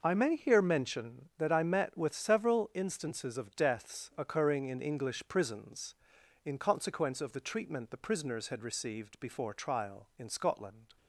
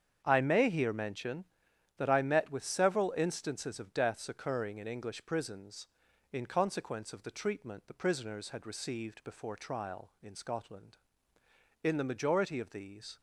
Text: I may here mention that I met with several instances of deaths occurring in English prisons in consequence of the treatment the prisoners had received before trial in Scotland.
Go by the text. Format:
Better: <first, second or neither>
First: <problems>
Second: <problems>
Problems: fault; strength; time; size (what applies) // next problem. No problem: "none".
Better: first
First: none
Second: starts louder than the rest; strong; until 1.2 s; 7.5 dB // goes on to say "In the majority of these"; from 11.8 s on; 1.3 s long